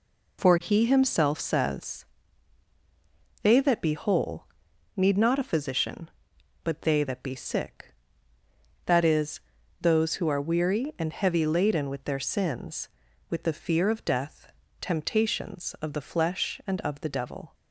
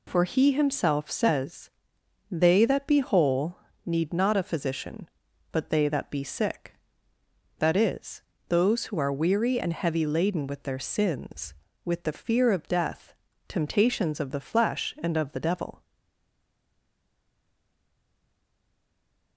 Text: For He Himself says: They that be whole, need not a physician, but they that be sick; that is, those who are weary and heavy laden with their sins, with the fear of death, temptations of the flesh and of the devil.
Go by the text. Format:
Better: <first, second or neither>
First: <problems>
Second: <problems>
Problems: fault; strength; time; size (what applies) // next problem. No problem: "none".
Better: first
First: none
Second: stays silent after the last word; strong; from 15.8 s on; 3.5 s long